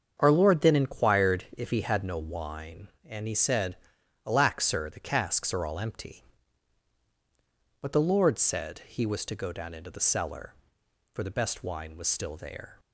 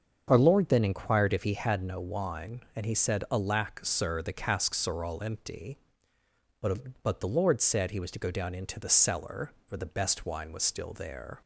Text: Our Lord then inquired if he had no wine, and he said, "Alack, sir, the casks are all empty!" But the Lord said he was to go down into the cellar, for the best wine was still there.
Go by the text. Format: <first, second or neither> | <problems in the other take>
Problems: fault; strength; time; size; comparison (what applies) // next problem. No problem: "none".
first | starts louder than the rest; until 1.2 s; 7 dB; also in the first // says "But" twice; at 7.0 s